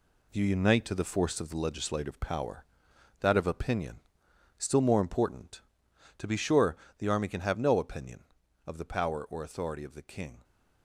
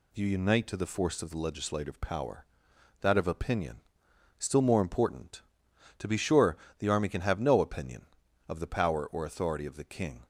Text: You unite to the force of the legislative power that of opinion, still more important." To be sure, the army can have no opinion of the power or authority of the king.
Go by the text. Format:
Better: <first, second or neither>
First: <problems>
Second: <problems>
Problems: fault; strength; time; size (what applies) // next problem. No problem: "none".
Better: second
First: gets quieter; strong; throughout; 8 dB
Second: none